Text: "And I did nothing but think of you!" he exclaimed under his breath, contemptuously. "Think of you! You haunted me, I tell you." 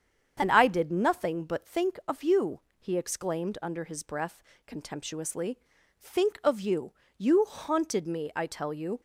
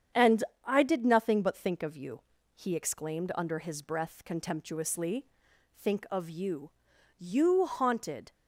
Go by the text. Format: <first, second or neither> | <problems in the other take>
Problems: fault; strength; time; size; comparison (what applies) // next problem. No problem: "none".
first | starts louder than the rest; strong; until 1.3 s; 8 dB; strong in the first // pauses between "And" and "I"; slight; at 0.4 s; 0.22 s long // stops before "me I tell you"; at 8.3 s